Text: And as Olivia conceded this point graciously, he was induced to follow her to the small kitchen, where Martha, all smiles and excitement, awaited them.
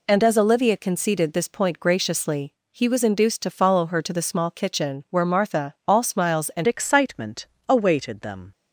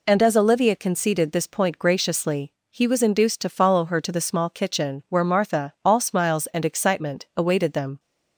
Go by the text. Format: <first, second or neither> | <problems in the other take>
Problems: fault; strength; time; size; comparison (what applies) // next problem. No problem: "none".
second | changes voice at "excitement"; from 6.6 s on; 1.8 s long